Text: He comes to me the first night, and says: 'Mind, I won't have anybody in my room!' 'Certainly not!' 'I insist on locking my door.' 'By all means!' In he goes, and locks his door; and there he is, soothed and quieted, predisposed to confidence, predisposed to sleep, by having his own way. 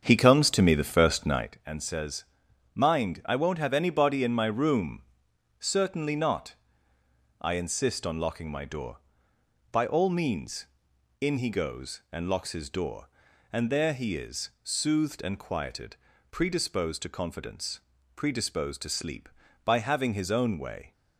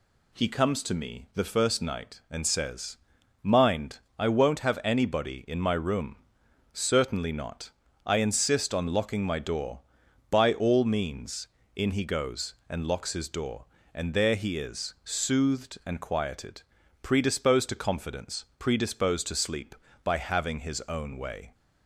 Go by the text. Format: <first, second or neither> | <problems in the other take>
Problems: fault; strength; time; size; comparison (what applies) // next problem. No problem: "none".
second | starts louder than the rest; strong; until 1.5 s; 7.5 dB